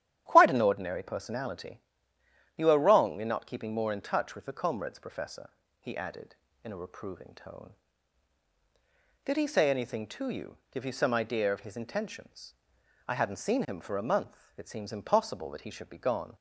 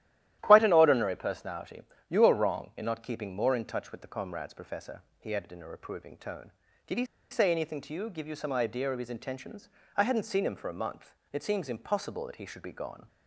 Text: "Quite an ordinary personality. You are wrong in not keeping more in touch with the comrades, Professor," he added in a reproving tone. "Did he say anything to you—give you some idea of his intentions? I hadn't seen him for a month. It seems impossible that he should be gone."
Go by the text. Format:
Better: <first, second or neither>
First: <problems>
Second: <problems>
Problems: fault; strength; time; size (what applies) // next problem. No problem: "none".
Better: first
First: starts louder than the rest; strong; until 1.2 s; 11 dB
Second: starts louder than the rest; strong; until 1.4 s; 13 dB // pauses between "he" and "say"; slight; at 7.0 s; 0.26 s long